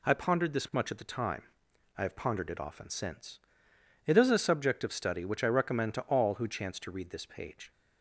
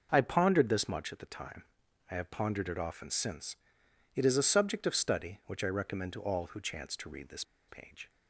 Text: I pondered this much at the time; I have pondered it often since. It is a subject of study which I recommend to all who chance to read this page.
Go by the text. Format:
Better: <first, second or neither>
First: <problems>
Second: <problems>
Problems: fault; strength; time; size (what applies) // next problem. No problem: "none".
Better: first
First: none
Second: pauses between "this" and "page"; slight; at 7.4 s; 0.24 s long